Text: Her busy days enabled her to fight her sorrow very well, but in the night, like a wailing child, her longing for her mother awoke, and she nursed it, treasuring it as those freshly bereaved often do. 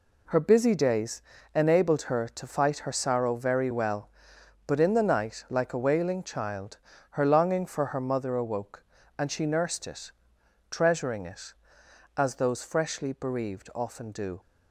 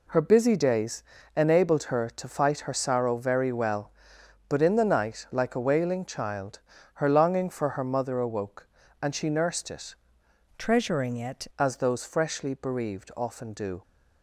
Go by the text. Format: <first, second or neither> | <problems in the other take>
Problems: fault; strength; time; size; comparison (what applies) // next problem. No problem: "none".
first | pauses between "days" and "enabled"; slight; at 1.0 s; 0.32 s long; slight in the first // changes voice from "treasuring" to "it"; from 10.5 to 11.4 s; 0.9 s long